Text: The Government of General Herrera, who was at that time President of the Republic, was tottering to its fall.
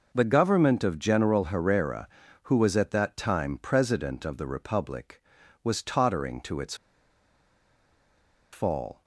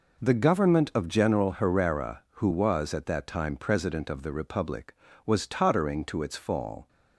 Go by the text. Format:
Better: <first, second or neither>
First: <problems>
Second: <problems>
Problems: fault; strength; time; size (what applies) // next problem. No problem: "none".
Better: second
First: pauses between "its" and "fall"; strong; at 6.7 s; 1.7 s long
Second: none